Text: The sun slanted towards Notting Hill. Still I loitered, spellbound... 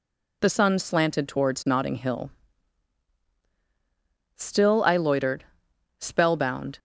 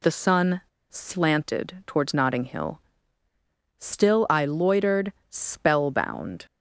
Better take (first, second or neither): first